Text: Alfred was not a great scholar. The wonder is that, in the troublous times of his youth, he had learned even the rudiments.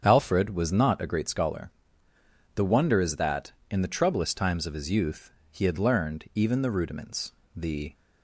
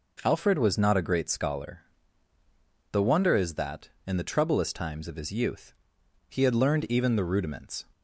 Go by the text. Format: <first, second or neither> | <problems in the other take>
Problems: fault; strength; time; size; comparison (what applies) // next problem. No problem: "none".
second | starts louder than the rest; strong; until 1.0 s; 7.5 dB // goes on to say "The"; slight; from 7.5 s on; 0.38 s long